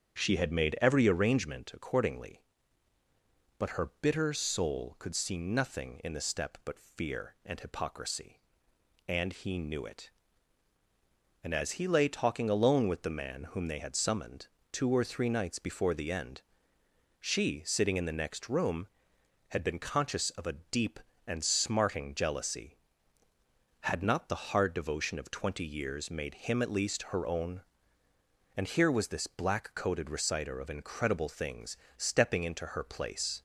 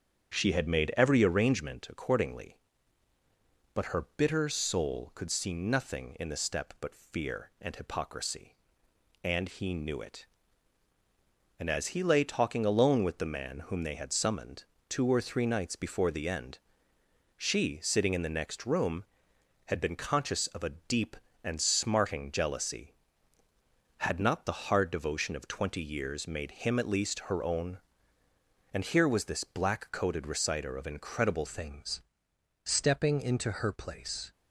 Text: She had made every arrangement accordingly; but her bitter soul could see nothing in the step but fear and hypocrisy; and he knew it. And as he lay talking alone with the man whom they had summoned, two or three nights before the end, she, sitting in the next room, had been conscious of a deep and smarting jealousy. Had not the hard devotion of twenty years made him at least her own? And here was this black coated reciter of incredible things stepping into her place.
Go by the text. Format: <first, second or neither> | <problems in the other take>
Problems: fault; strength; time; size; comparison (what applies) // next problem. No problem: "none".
first | starts louder than the rest; strong; until 1.3 s; 7.5 dB; strong in the first // changes voice at "things"; from 31.4 s on; 2.9 s long // pauses between "things" and "stepping"; noticeable; at 32.0 s; 0.64 s long; slight in the first